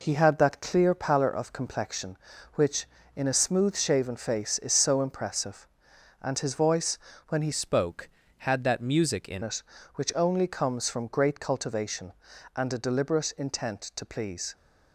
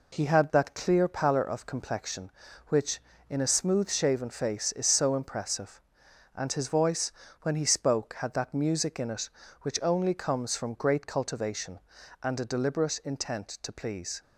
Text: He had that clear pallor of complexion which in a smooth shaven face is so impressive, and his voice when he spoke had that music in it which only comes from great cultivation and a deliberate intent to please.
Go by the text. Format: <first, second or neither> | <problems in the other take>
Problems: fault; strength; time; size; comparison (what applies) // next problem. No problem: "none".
second | pauses between "voice" and "when"; slight; at 6.9 s; 0.30 s long; slight in the second // changes voice from "spoke" to "in"; from 7.5 to 9.4 s; 1.9 s long